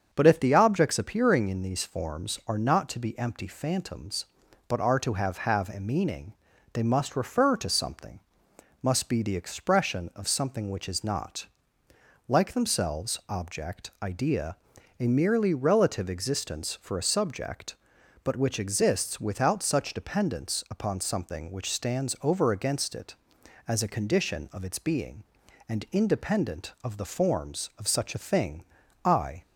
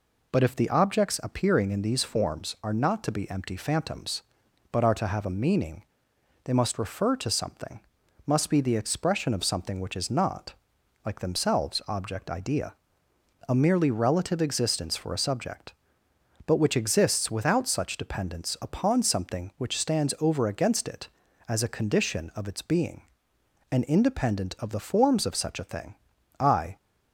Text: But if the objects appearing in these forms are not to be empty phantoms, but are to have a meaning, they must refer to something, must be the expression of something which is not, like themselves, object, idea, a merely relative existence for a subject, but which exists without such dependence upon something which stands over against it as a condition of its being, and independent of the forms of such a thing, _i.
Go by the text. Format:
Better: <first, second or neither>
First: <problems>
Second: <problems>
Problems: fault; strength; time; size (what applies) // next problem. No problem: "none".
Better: second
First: starts louder than the rest; strong; until 1.1 s; 7.5 dB // says "have" twice; at 5.3 s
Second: none